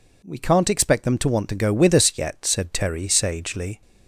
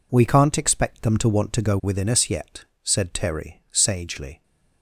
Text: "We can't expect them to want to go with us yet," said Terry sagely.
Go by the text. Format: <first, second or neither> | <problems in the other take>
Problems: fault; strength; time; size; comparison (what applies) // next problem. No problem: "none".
first | says "within" for "with"; at 1.8 s